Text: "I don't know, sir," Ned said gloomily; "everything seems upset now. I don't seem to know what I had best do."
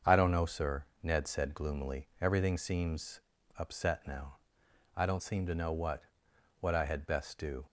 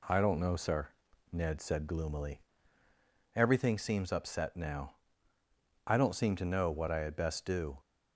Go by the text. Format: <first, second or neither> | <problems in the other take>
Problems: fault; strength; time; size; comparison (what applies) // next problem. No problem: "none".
second | starts louder than the rest; until 1.2 s; 7 dB // pauses between "seems" and "upset"; slight; at 3.2 s; 0.36 s long // says "what" twice; at 6.5 s